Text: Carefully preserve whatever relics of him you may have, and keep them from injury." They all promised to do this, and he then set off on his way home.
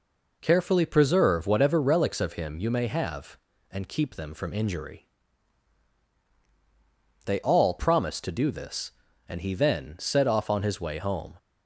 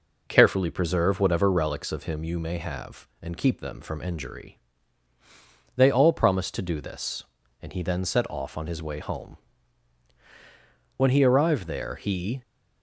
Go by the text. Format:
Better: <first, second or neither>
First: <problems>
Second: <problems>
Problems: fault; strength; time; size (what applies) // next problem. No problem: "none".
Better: first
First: none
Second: goes on to say "When he arrived there he"; from 10.9 s on; 1.4 s long